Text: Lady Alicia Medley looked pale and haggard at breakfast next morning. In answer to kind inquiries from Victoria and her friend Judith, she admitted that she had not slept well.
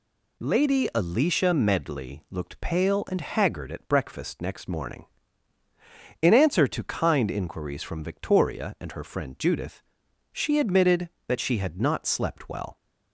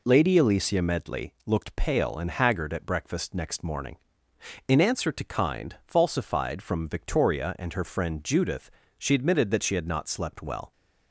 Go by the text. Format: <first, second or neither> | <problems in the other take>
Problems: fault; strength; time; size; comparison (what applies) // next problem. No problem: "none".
first | says "falsified" for "inquiries"; at 5.8 s